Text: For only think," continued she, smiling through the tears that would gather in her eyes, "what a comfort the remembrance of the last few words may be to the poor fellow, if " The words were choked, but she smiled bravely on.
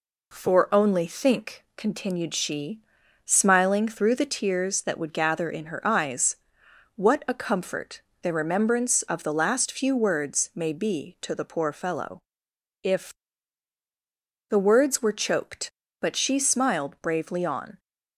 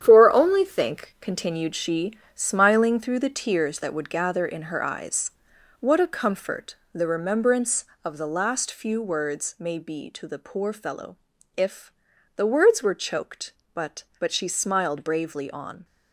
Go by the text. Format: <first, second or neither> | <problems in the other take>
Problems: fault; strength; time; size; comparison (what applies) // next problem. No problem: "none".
first | starts louder than the rest; strong; until 1.0 s; 9.5 dB // pauses between "comfort" and "the"; slight; at 6.7 s; 0.16 s long; slight in the first // says "but" twice; at 14.1 s